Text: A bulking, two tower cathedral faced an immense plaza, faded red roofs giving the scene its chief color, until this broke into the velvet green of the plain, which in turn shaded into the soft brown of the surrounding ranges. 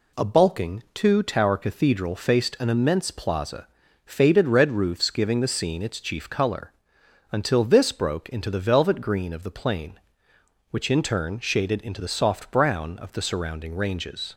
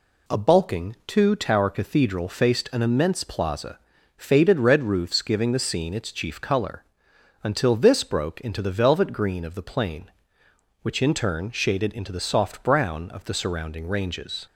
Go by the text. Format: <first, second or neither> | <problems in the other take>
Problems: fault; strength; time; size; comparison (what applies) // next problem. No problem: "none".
neither | none